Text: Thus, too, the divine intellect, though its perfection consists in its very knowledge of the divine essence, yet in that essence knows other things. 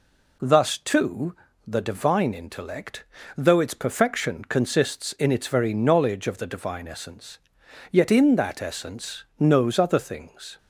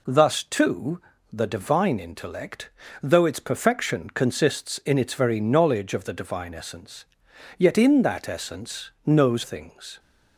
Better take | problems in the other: first | pauses between "essence" and "knows"; slight; at 8.8 s; 0.16 s long; slight in the first // skips "other"; at 9.4 s

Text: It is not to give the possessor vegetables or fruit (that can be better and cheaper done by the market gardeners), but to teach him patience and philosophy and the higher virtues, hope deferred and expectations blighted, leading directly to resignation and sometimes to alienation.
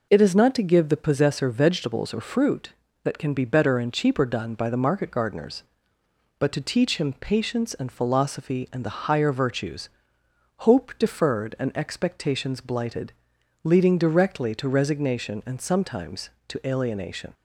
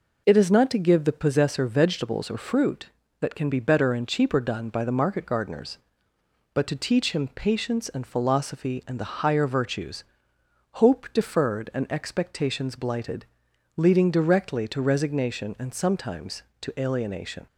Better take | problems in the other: neither | none

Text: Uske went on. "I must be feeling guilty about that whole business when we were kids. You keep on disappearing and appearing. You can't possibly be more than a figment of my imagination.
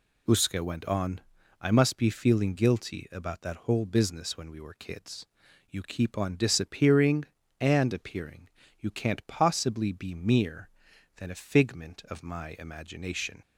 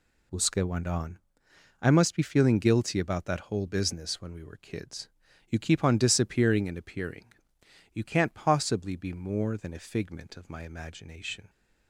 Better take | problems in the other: second | says "mere" for "more"; at 10.1 s

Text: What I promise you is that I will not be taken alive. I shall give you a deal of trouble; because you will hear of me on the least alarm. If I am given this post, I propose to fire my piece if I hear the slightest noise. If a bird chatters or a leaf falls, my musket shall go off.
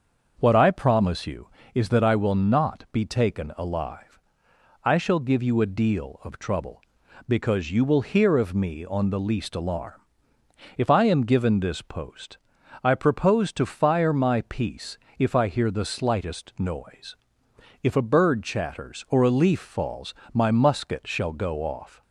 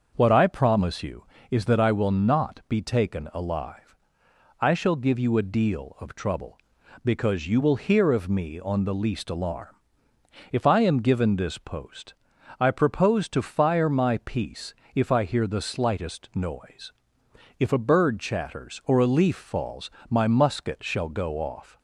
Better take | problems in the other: neither | starts louder than the rest; the same in both // pauses between "piece" and "if"; slight; the same in both

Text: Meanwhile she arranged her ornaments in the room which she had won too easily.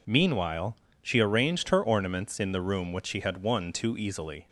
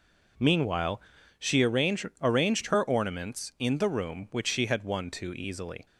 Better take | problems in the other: first | pauses between "Meanwhile" and "she"; at 0.9 s; 0.40 s long; slight in the first // says "arranged" twice; at 2.2 s

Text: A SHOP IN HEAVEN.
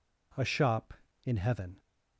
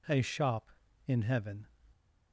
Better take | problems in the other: neither | none

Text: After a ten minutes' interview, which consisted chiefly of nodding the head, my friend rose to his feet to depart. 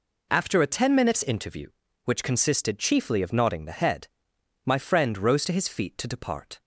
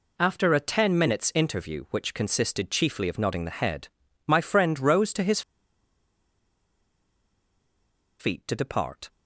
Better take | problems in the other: first | pauses between "his" and "feet"; strong; at 5.4 s; 2.7 s long

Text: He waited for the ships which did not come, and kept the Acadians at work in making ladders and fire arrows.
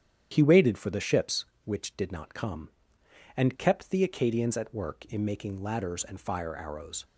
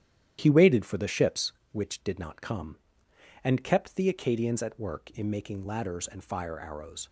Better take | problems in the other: first | gets quieter; noticeable; throughout; 6 dB // starts louder than the rest; strong; until 1.4 s; 11 dB; strong in the first

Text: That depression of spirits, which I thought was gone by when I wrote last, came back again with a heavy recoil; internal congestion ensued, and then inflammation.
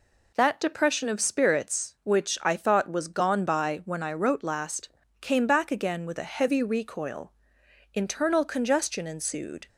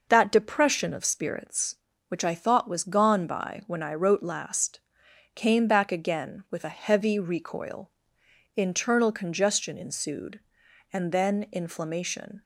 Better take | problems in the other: second | stops before "and then inflammation"; at 9.6 s

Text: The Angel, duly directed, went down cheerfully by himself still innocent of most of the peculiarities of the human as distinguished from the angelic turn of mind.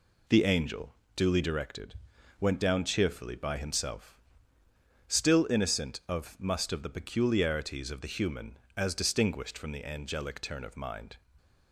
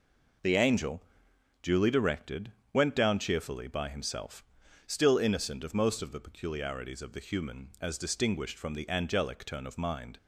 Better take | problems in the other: second | pauses between "himself" and "still"; noticeable; at 4.1 s; 0.96 s long; also in the second // says "must" for "most"; at 6.3 s

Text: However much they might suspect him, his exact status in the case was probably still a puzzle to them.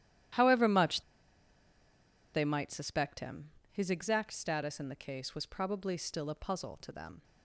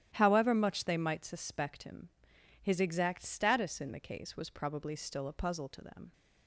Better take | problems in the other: second | starts louder than the rest; strong; until 2.6 s; 12 dB; strong in the second // pauses between "much" and "they"; strong; at 1.0 s; 1.3 s long

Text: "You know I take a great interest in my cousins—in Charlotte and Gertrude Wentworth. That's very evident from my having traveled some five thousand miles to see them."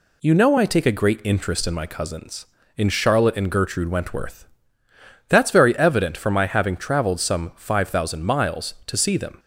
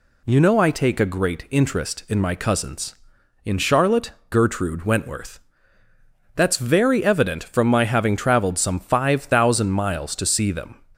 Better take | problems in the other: first | skips "and"; at 4.2 s

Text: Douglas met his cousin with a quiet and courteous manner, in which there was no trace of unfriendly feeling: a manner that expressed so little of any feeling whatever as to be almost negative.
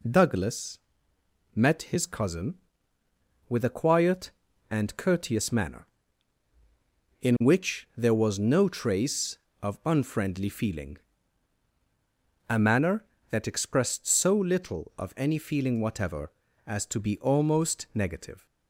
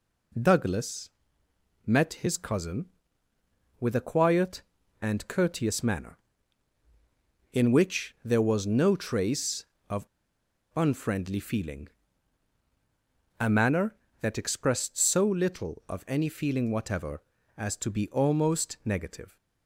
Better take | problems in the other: first | pauses between "Douglas" and "met"; noticeable; at 1.1 s; 0.74 s long; noticeable in the first // pauses between "of" and "unfriendly"; noticeable; at 10.0 s; 0.67 s long

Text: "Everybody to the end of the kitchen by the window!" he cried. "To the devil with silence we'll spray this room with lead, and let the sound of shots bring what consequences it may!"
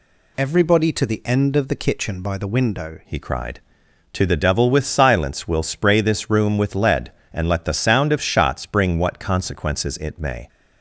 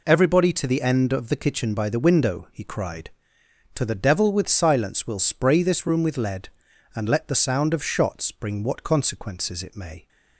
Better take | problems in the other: second | changes voice at "he"; from 3.0 s on; 7.4 s long

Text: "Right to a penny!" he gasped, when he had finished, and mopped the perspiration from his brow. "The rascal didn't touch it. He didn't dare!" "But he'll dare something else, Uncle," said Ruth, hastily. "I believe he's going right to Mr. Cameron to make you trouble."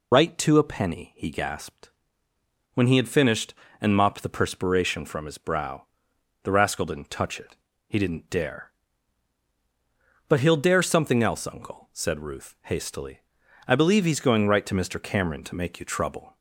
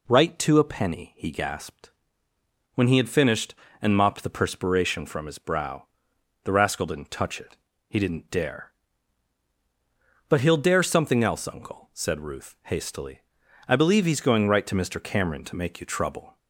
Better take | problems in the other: second | loses the start of "Right"; at 0.1 s; 50 ms

